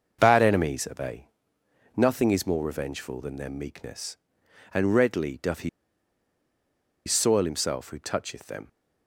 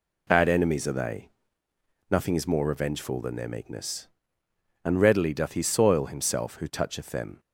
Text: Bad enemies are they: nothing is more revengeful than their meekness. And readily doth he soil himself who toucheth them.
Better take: second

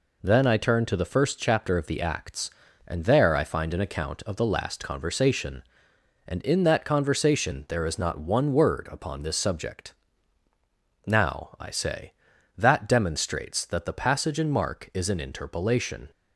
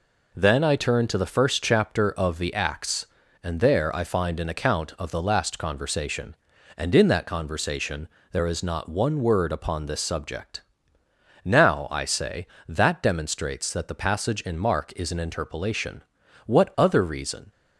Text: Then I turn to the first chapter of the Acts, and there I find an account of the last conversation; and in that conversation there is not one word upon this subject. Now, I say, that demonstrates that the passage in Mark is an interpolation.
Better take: first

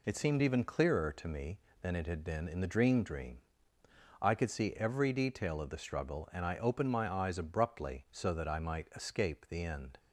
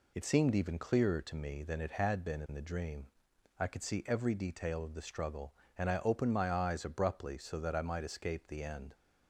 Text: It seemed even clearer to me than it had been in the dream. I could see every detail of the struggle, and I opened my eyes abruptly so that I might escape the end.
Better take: second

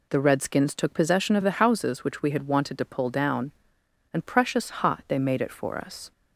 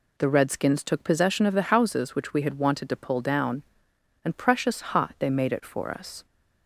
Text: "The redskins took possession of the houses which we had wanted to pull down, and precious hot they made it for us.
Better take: neither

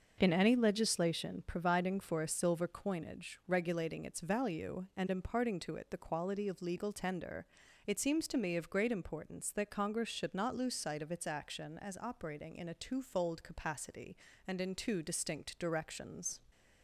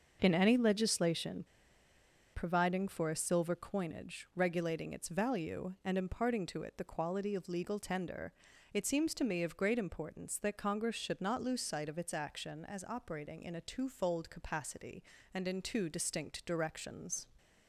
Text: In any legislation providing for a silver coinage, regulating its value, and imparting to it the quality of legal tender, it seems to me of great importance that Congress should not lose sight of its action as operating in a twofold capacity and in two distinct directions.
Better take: first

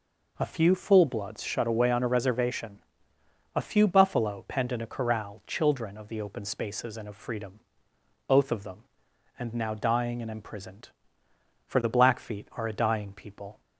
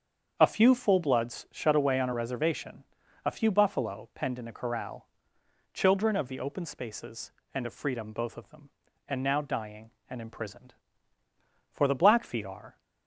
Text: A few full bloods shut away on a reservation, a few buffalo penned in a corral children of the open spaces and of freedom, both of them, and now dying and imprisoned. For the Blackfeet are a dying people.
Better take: first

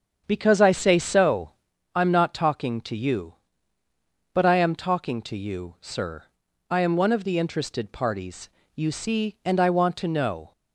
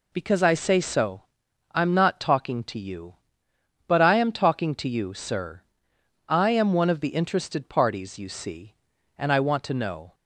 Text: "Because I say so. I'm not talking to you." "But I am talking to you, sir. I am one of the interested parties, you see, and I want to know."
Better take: second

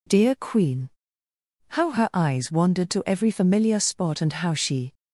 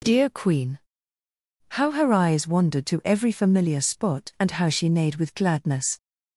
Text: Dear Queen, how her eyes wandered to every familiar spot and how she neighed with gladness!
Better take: second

